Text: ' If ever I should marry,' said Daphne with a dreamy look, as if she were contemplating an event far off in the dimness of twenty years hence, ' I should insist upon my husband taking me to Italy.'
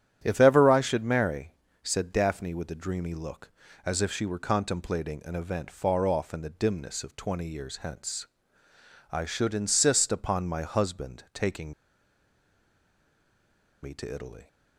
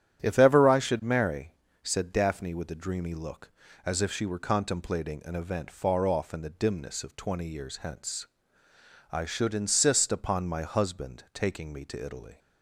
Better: second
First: starts louder than the rest; strong; until 1.2 s; 11 dB // pauses between "taking" and "me"; strong; at 11.7 s; 2.1 s long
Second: starts louder than the rest; strong; until 1.2 s; 11 dB

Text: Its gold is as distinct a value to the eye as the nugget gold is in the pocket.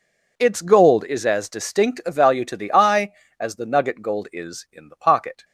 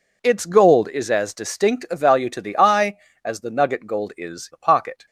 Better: first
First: none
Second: skips "in"; at 4.5 s

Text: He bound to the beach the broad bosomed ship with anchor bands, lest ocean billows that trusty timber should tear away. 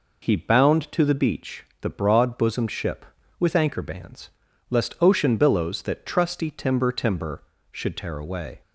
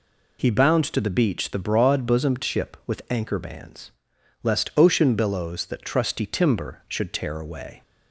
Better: second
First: pauses between "beach" and "the"; slight; at 1.6 s; 0.16 s long // says "timber" twice; at 6.9 s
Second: none

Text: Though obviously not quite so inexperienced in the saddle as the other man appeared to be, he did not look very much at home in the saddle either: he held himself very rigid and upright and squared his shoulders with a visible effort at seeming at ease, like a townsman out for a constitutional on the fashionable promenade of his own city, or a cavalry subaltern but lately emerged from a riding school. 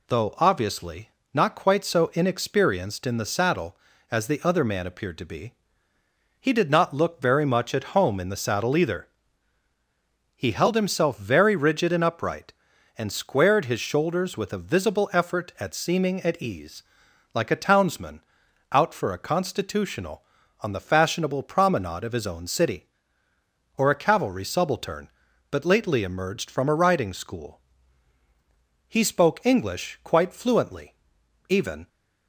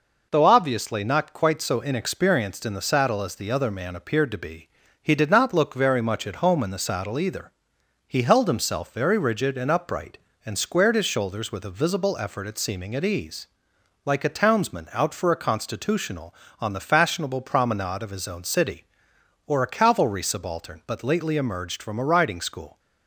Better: second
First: pauses between "obviously" and "not"; slight; at 1.0 s; 0.24 s long // pauses between "townsman" and "out"; noticeable; at 18.2 s; 0.50 s long // goes on to say "He spoke English quite fluently even"; strong; from 28.8 s on; 3.0 s long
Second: none

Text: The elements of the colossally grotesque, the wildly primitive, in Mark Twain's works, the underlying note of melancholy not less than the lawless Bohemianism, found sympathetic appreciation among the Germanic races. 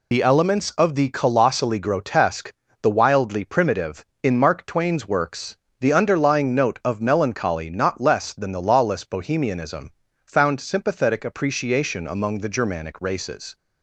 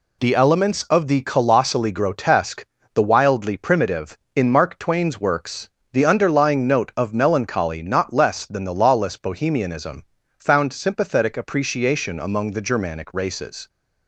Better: second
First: loses the start of "The"; at 0.1 s; 30 ms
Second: none

